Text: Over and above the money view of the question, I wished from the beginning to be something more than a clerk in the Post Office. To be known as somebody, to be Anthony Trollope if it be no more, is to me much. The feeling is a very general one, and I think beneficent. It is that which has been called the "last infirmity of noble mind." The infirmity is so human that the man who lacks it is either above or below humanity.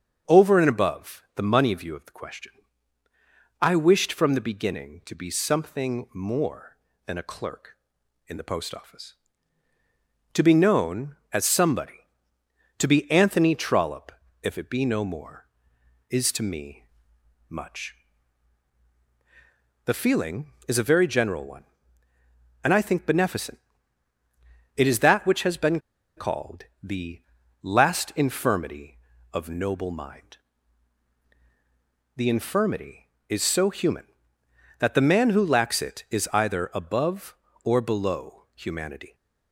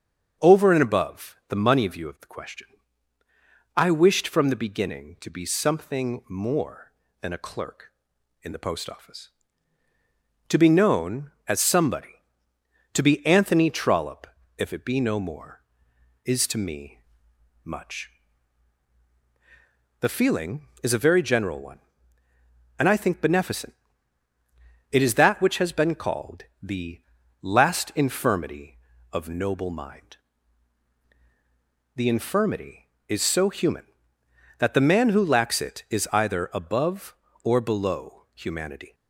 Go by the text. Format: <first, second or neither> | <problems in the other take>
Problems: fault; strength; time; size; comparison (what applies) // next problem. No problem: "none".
second | starts louder than the rest; until 1.3 s; 6.5 dB; also in the second // pauses between "Trollope" and "if"; slight; at 14.1 s; 0.30 s long; slight in the second // pauses between "me" and "much"; noticeable; at 16.8 s; 0.62 s long; noticeable in the second // pauses between "been" and "called"; at 25.7 s; 0.37 s long // pauses between "called" and "the"; slight; at 26.6 s; 0.18 s long; slight in the second // pauses between "the" and "last"; at 27.2 s; 0.42 s long; also in the second